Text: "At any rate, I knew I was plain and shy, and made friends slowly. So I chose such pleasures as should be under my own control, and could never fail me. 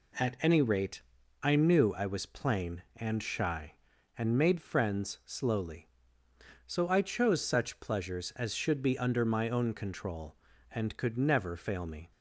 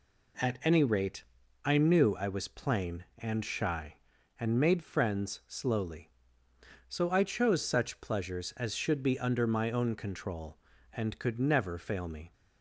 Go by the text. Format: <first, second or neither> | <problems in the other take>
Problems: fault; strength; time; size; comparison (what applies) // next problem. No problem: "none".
neither | none